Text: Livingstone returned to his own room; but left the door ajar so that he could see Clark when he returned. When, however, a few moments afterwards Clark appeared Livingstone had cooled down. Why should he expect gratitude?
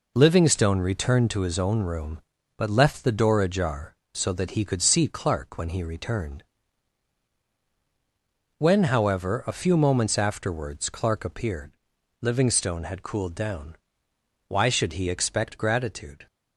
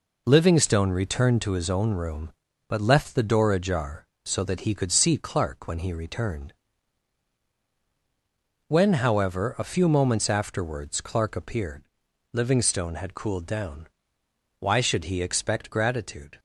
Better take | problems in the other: neither | pauses between "appeared" and "Livingstone"; noticeable; the same in both

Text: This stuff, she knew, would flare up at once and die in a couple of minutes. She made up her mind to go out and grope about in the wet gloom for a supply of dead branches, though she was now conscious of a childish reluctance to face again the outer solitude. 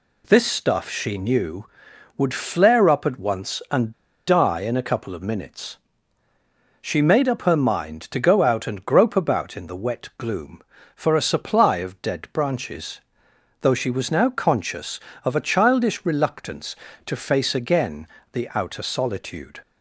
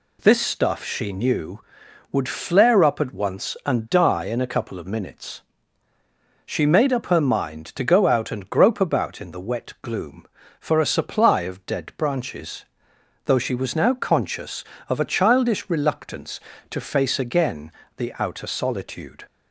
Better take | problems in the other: second | pauses between "and" and "die"; slight; at 3.9 s; 0.35 s long // pauses between "again" and "the"; slight; at 18.0 s; 0.26 s long; slight in the second

